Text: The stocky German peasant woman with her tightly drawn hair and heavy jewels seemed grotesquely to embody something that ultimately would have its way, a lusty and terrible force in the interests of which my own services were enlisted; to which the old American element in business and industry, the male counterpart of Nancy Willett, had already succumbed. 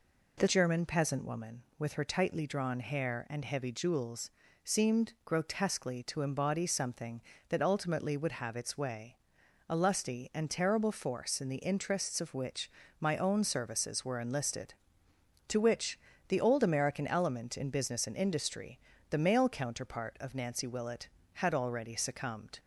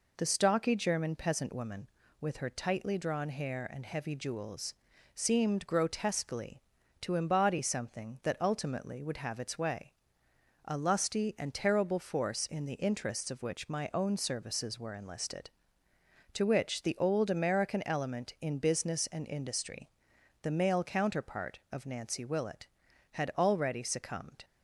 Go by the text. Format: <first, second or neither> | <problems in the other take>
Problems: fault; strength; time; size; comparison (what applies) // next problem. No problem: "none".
second | skips "stocky"; at 0.4 s // pauses between "jewels" and "seemed"; slight; at 4.3 s; 0.32 s long; also in the second // pauses between "which" and "my"; slight; at 12.7 s; 0.28 s long // pauses between "which" and "the"; slight; at 15.9 s; 0.30 s long